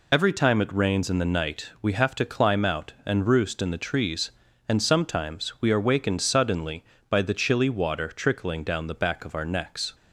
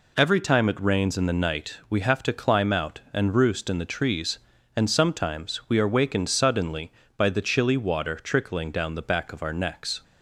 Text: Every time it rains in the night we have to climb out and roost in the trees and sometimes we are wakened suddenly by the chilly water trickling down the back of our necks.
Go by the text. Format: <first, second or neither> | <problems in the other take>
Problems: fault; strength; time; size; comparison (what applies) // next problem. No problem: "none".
second | loses the start of "Every"; at 0.1 s; 35 ms